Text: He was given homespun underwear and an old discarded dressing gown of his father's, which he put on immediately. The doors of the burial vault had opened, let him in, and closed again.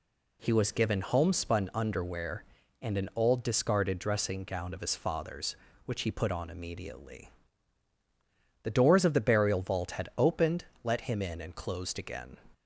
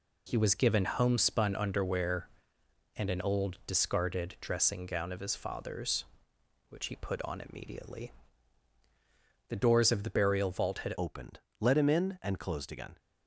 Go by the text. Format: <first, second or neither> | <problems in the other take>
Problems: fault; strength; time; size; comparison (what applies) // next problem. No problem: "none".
first | changes voice at "opened"; from 10.9 s on; 2.0 s long